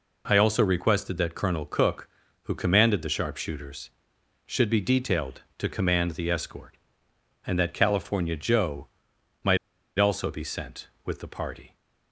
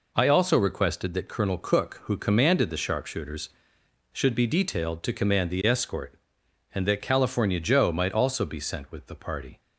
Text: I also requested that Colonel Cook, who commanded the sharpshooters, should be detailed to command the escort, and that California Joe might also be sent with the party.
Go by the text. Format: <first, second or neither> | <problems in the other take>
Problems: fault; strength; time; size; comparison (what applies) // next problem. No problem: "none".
second | pauses between "Joe" and "might"; noticeable; at 8.8 s; 0.56 s long // pauses between "might" and "also"; at 9.5 s; 0.41 s long